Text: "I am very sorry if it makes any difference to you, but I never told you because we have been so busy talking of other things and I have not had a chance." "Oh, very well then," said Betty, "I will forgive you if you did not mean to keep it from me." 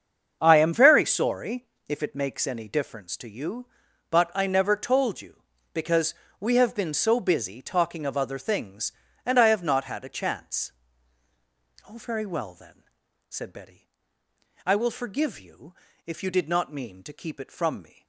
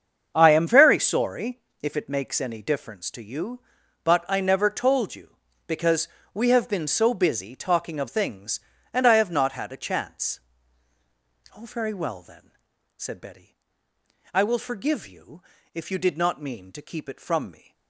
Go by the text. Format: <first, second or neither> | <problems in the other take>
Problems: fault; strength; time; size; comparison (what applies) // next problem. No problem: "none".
first | starts louder than the rest; until 1.3 s; 7 dB; also in the first // pauses between "sorry" and "if"; slight; at 1.5 s; 0.24 s long; slight in the first // pauses between "because" and "we"; slight; at 6.0 s; 0.26 s long; slight in the first // skips "other"; at 8.0 s // pauses between "you" and "if"; slight; at 15.4 s; 0.32 s long; slight in the first